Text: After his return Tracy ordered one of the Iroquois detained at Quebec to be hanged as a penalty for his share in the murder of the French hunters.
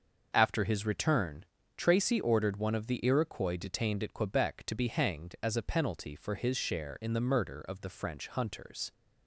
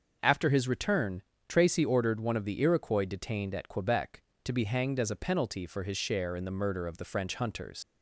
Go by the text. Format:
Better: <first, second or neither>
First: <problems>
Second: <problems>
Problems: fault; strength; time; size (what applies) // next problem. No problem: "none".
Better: first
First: starts louder than the rest; until 1.3 s; 6.5 dB // pauses between "return" and "Tracy"; slight; at 1.4 s; 0.32 s long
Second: starts louder than the rest; noticeable; until 1.2 s; 6 dB // pauses between "return" and "Tracy"; slight; at 1.2 s; 0.26 s long // leaves "hunters" unfinished; at 7.8 s; 105 ms